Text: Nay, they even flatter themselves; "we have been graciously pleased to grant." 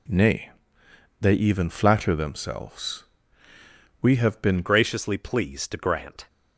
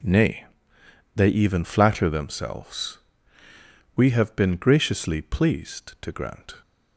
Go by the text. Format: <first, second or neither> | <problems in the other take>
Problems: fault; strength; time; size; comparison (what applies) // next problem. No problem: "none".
second | changes voice at "graciously"; from 4.6 s on; 1.6 s long